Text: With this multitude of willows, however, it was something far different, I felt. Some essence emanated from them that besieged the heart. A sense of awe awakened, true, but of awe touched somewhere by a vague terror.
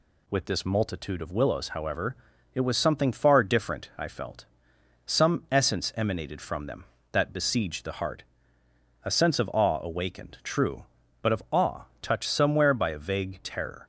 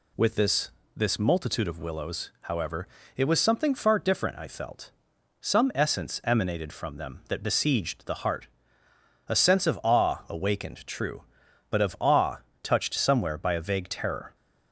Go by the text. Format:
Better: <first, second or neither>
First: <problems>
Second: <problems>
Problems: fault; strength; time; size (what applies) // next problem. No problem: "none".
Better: first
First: pauses between "awe" and "touched"; slight; at 11.8 s; 0.20 s long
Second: says "this" twice; at 0.9 s // pauses between "awe" and "touched"; slight; at 12.3 s; 0.26 s long